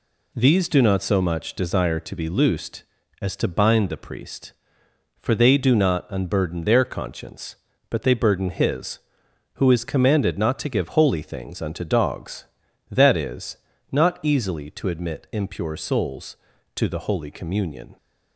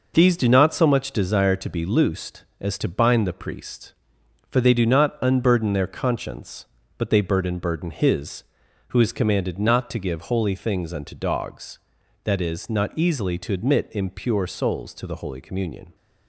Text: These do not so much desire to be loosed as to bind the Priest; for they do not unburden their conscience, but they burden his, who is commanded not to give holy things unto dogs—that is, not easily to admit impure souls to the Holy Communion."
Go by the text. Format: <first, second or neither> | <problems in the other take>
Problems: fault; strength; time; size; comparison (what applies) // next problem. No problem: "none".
first | says "burden" twice; at 7.5 s